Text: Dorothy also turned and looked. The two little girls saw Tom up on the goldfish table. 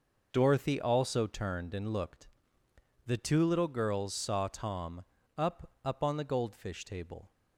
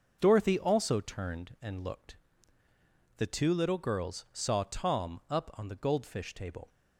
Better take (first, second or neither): second